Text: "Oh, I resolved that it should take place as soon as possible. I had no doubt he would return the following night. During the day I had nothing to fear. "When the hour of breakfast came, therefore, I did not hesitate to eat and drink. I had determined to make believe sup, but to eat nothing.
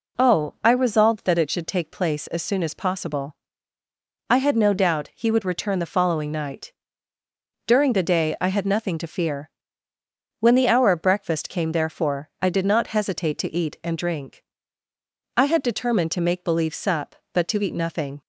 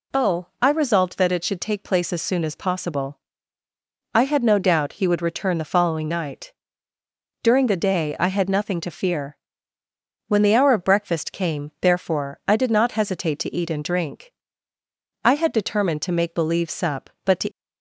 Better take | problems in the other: first | stops before "eat nothing"; at 17.5 s

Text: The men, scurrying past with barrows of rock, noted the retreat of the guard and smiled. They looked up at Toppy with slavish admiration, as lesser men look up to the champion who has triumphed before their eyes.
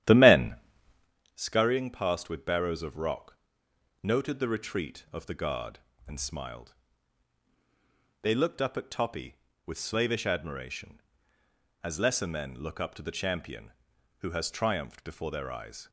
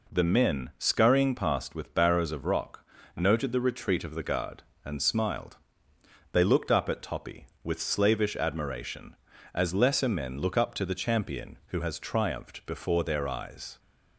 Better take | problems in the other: second | starts louder than the rest; strong; until 1.1 s; 11.5 dB

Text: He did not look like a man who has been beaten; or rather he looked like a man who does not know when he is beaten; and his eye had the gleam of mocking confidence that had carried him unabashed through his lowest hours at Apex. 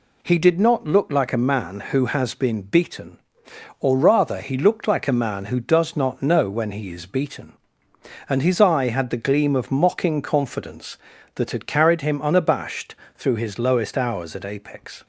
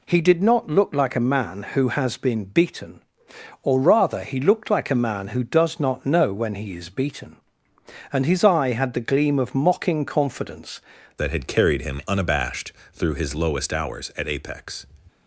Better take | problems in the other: first | changes voice at "that"; from 11.1 s on; 3.7 s long // pauses between "unabashed" and "through"; slight; at 12.7 s; 0.22 s long; slight in the first

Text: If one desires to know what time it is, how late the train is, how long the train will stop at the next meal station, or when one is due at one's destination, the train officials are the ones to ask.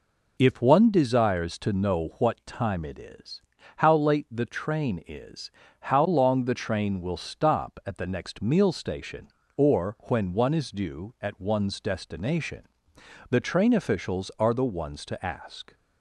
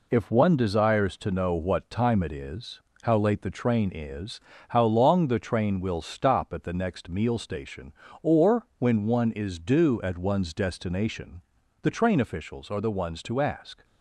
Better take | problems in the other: first | gets quieter; noticeable; throughout; 5.5 dB

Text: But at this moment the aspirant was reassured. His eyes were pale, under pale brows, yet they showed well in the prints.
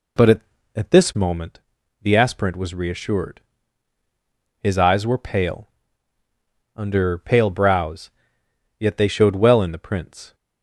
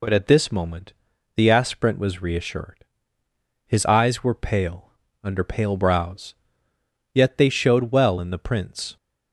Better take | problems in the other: second | says "at" twice; at 0.7 s // pauses between "moment" and "the"; at 1.6 s; 0.42 s long; noticeable in the second

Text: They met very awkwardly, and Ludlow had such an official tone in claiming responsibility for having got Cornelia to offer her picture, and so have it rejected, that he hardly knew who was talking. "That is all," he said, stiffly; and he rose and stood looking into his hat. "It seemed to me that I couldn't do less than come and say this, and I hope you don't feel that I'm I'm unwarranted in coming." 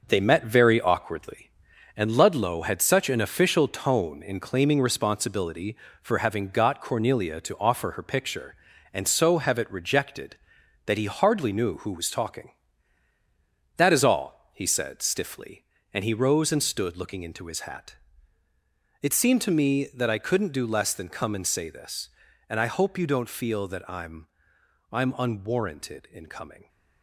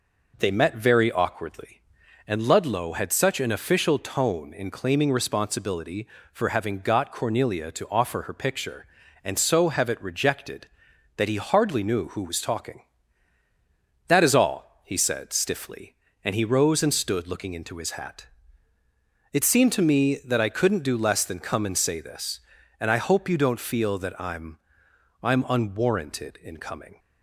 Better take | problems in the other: second | gets quieter; strong; throughout; 7 dB // pauses between "I'm" and "I'm"; noticeable; at 24.2 s; 0.64 s long; noticeable in the second

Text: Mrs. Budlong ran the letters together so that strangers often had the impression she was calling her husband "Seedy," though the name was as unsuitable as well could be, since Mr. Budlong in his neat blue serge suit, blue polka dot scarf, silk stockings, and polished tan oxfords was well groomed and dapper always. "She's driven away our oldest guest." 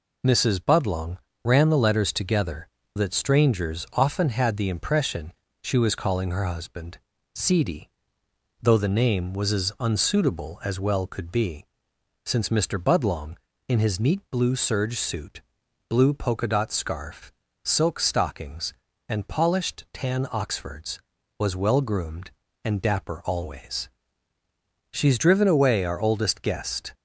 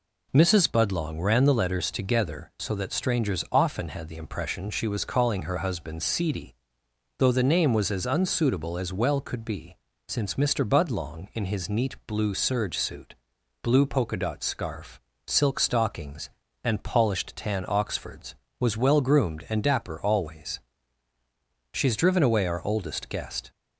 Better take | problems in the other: second | pauses between "Budlong" and "ran"; slight; at 1.1 s; 0.26 s long // skips "so"; at 2.8 s // pauses between "impression" and "she"; slight; at 5.3 s; 0.32 s long // pauses between "husband" and "Seedy"; slight; at 6.9 s; 0.34 s long

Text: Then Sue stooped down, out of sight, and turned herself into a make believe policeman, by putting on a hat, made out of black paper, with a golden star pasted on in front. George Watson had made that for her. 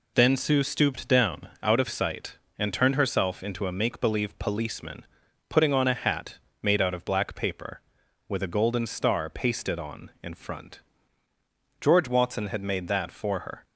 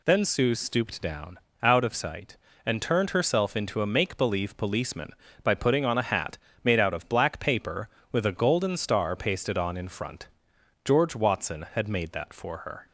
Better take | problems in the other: second | skips "by"; at 5.2 s

